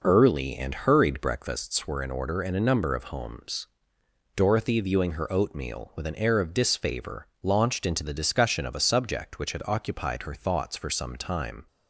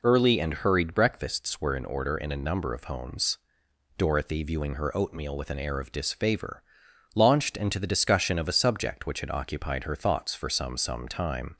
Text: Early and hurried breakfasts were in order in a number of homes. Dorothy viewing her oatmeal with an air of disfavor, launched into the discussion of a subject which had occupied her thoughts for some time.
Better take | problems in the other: first | says "some" twice; at 10.7 s

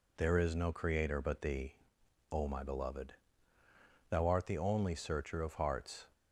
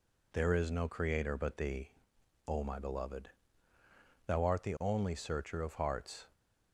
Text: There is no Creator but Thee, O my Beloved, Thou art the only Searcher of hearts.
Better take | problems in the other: neither | none

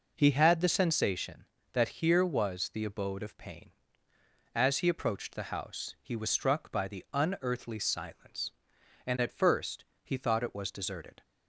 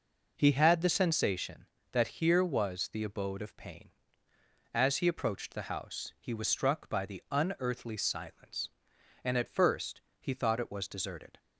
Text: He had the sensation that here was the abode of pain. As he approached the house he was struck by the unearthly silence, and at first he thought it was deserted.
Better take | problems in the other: neither | pauses between "first" and "he"; slight; the same in both

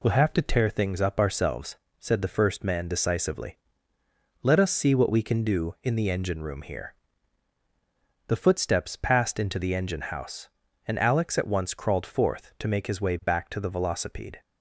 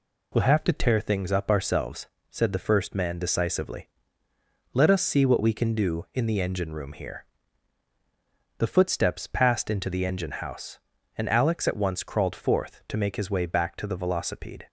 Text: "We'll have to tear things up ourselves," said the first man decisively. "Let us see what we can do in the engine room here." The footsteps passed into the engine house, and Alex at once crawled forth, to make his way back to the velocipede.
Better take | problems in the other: neither | none

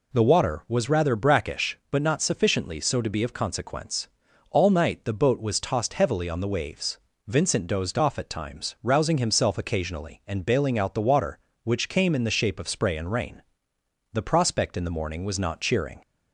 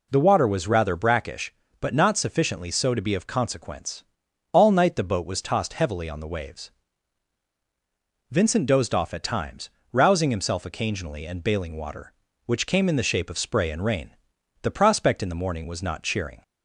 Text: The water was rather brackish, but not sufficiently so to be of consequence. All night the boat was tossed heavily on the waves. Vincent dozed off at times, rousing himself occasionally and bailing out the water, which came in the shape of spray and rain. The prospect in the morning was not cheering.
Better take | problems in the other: first | skips "out the"; at 11.7 s

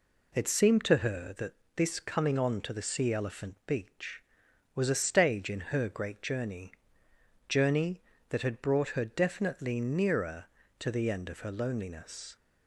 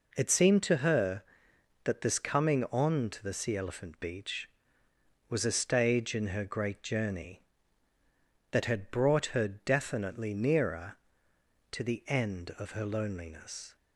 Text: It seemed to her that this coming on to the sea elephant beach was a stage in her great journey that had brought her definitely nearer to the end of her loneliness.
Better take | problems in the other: second | pauses between "that" and "this"; slight; at 1.5 s; 0.22 s long // says "journey" twice; at 7.4 s

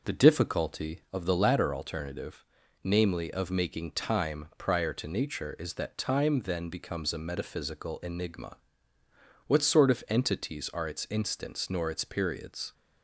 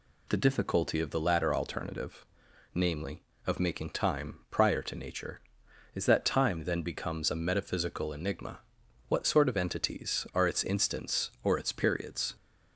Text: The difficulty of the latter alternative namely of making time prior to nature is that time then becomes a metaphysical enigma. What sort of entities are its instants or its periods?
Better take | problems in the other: second | pauses between "alternative" and "namely"; at 2.4 s; 0.42 s long; noticeable in the second // says "nor" for "or"; at 11.6 s

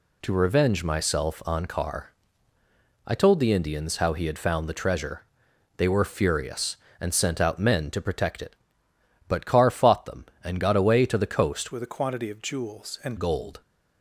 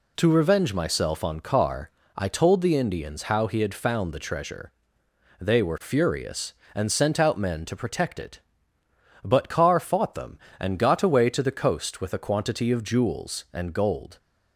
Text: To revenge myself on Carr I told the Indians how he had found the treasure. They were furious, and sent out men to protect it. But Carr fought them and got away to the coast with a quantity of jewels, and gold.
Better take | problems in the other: second | pauses between "Carr" and "I"; noticeable; at 2.1 s; 0.94 s long; slight in the second // changes voice from "with" to "and"; from 11.7 to 13.1 s; 1.4 s long

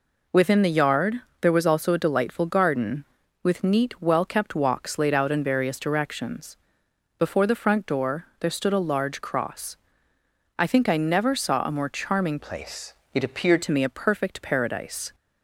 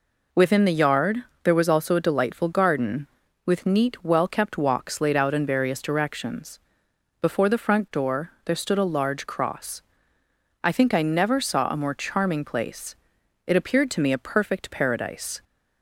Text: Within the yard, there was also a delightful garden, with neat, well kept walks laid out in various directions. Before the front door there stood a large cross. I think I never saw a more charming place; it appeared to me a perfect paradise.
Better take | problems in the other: second | changes voice from "place" to "appeared"; from 12.3 to 13.6 s; 1.3 s long

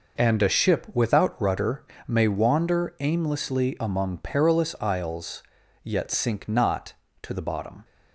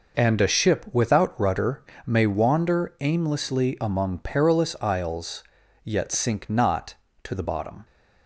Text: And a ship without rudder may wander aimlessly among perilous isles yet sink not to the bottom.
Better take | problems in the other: neither | pauses between "rudder" and "may"; slight; the same in both // pauses between "isles" and "yet"; the same in both

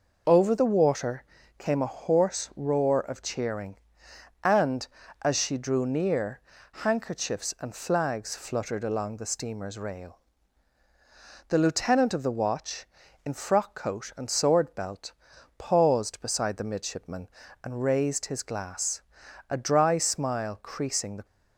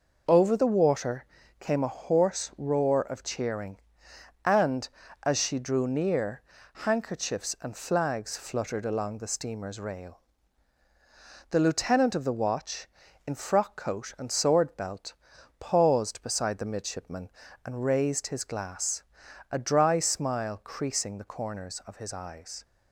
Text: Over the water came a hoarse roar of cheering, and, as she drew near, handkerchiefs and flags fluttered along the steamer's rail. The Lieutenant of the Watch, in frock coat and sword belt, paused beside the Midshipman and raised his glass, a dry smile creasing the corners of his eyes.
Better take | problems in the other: second | pauses between "water" and "came"; slight; at 1.2 s; 0.34 s long; slight in the second // stops before "corners of his eyes"; at 21.2 s

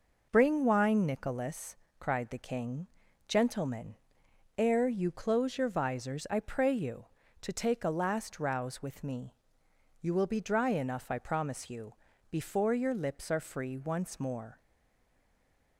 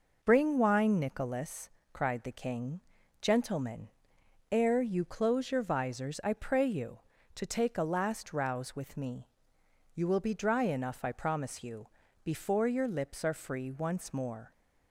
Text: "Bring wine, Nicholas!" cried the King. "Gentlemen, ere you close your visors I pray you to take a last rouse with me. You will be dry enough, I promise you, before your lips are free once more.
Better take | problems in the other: second | stays silent after the last word; noticeable; from 14.5 s on; 1.2 s long

